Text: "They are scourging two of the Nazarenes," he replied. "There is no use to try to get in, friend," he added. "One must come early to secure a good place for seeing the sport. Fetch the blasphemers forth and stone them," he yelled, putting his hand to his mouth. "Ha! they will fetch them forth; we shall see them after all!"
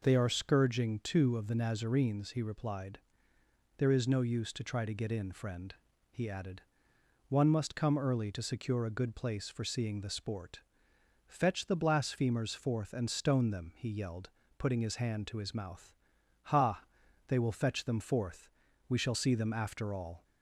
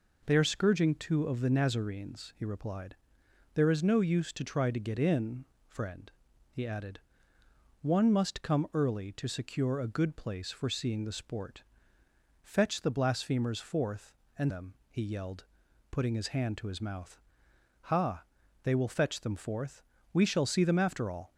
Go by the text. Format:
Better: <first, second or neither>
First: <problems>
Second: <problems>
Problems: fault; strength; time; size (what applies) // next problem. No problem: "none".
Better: first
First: none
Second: skips "stone"; at 14.5 s